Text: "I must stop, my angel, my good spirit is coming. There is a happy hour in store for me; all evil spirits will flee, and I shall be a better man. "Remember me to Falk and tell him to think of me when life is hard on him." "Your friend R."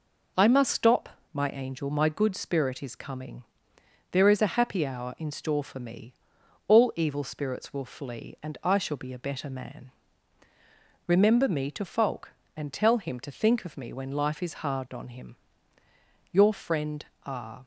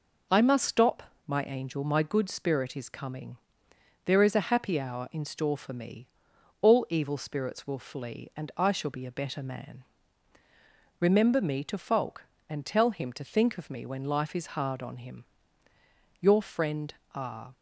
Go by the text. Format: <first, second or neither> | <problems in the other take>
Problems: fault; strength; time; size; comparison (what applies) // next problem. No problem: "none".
neither | pauses between "friend" and "R"; slight; the same in both